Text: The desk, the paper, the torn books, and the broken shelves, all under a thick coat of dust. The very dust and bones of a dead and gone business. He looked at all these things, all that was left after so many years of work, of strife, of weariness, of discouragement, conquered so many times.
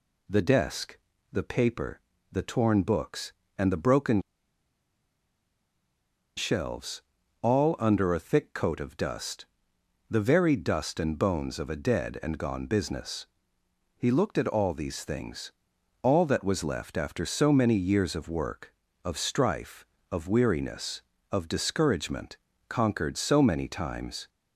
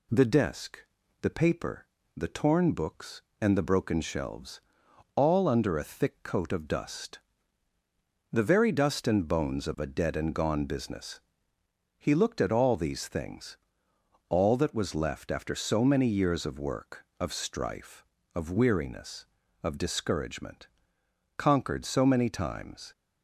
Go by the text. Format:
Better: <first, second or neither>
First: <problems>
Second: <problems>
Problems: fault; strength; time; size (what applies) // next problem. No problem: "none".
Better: second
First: pauses between "broken" and "shelves"; strong; at 4.2 s; 2.1 s long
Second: none